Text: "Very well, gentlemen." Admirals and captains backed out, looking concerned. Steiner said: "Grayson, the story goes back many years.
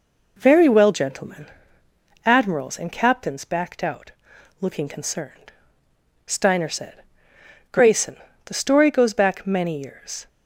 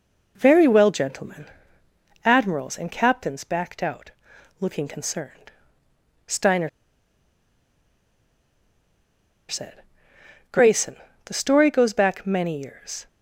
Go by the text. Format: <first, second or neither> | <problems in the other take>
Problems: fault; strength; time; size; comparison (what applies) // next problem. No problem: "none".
first | pauses between "Steiner" and "said"; strong; at 6.6 s; 2.8 s long